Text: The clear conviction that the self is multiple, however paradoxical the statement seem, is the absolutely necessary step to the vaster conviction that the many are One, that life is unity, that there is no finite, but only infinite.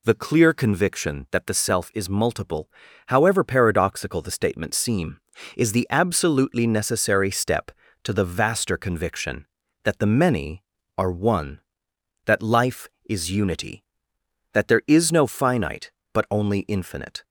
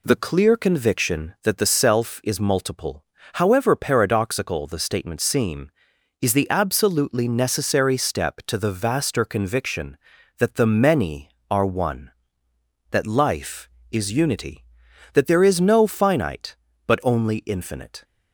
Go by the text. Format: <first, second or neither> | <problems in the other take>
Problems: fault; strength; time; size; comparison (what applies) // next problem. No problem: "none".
neither | none